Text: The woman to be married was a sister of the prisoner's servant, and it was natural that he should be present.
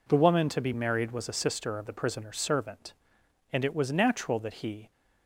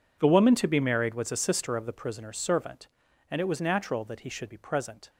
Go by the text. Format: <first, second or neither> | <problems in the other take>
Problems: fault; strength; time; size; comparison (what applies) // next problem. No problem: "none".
second | stops before "should be present"; at 4.9 s